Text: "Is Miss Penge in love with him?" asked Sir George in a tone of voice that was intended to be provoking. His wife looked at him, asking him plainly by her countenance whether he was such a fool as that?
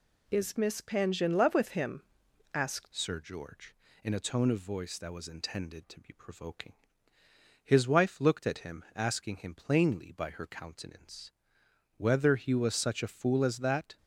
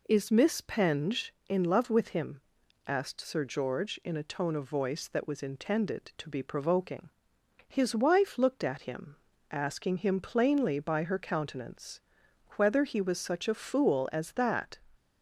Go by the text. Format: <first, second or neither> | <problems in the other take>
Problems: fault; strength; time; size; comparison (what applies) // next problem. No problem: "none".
second | changes voice at "Sir"; from 2.9 s on; 11.0 s long // pauses between "countenance" and "whether"; noticeable; at 11.3 s; 0.64 s long; noticeable in the second